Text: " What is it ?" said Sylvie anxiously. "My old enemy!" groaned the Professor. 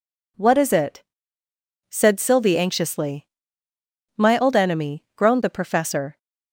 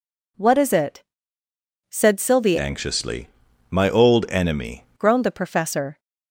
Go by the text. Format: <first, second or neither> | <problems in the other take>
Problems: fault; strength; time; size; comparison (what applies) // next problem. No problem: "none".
first | changes voice from "anxiously" to "enemy"; from 2.5 to 4.8 s; 2.3 s long